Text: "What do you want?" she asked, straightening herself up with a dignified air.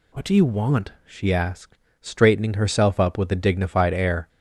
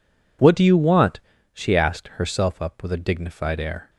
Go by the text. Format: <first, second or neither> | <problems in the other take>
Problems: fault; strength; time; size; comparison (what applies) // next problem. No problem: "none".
first | skips "straightening"; at 2.1 s